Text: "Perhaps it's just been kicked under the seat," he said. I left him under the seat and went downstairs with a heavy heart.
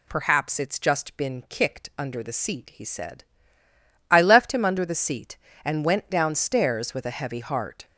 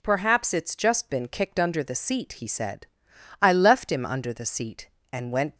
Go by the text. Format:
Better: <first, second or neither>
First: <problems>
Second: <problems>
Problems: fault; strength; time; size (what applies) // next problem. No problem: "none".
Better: first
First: none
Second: stops before "downstairs with a heavy heart"; at 5.5 s